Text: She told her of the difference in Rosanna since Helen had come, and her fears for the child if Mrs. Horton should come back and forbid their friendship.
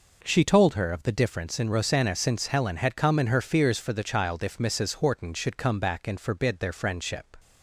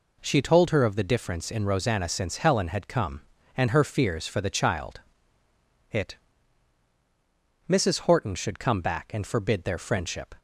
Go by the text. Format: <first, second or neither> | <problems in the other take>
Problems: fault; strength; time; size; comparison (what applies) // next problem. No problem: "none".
first | says "it" for "if"; at 5.9 s